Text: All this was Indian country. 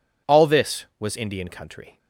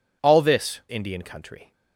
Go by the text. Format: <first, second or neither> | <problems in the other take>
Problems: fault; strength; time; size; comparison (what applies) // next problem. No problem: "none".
first | skips "was"; at 0.8 s